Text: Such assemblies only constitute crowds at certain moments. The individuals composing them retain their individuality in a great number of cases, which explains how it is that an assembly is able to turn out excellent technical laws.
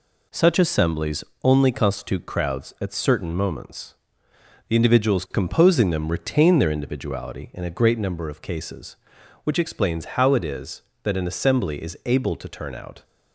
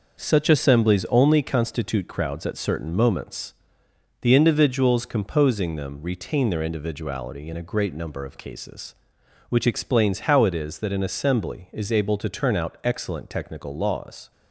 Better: second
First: pauses between "assemblies" and "only"; slight; at 1.2 s; 0.20 s long // stops before "excellent technical laws"; at 13.0 s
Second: none

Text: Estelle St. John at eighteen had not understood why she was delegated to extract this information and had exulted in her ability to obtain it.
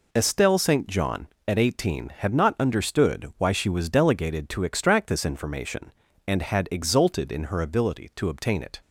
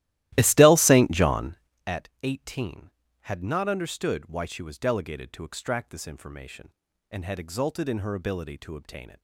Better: first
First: none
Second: starts louder than the rest; strong; until 1.8 s; 15.5 dB // pauses between "at" and "eighteen"; slight; at 2.0 s; 0.16 s long

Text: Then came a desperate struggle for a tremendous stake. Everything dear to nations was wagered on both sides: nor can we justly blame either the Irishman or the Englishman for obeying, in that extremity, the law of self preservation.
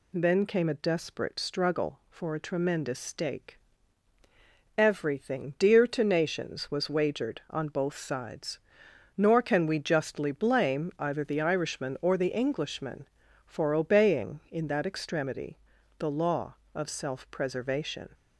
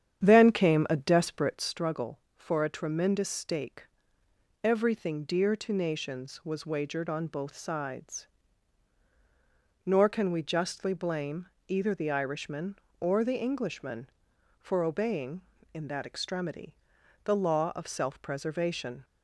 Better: first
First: none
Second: starts louder than the rest; strong; until 1.8 s; 9 dB // pauses between "blame" and "either"; slight; at 11.4 s; 0.18 s long

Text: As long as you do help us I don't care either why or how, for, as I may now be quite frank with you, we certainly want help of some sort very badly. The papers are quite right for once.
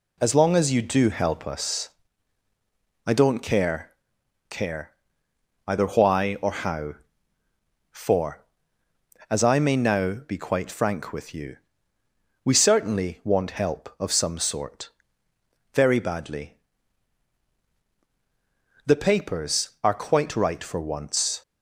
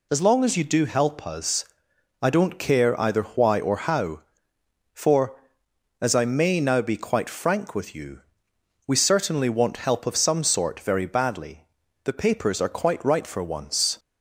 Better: second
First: pauses between "us" and "I"; at 1.8 s; 1.1 s long // says "care" twice; at 4.4 s // pauses between "sort" and "very"; noticeable; at 14.8 s; 0.84 s long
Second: pauses between "us" and "I"; noticeable; at 1.6 s; 0.56 s long

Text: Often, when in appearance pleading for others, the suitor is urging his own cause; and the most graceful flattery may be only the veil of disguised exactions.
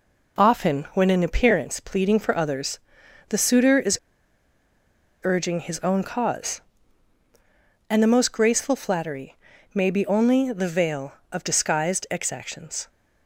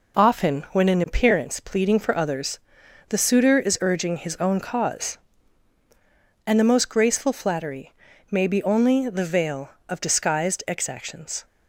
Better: second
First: pauses between "is" and "urging"; strong; at 3.9 s; 1.2 s long // pauses between "flattery" and "may"; at 9.3 s; 0.38 s long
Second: pauses between "flattery" and "may"; at 7.9 s; 0.38 s long

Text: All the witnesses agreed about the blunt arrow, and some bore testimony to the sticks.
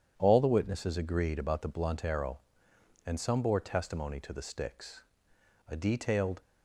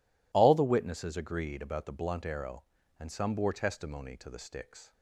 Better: second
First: goes on to say "A detailed"; noticeable; from 5.6 s on; 0.74 s long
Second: none

